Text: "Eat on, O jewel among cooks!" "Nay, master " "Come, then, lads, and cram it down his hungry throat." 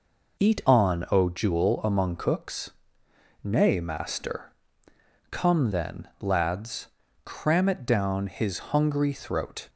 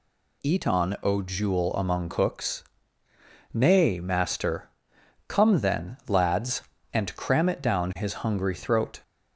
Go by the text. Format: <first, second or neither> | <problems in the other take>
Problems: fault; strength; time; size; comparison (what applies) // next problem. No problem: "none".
second | skips "and"; at 7.0 s